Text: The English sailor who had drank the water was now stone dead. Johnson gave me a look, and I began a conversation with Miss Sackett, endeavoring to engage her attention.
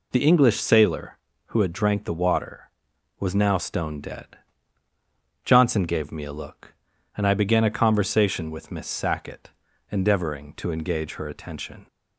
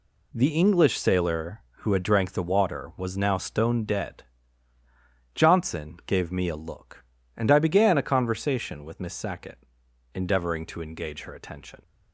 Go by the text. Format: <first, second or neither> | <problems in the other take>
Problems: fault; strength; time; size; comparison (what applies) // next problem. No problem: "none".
neither | none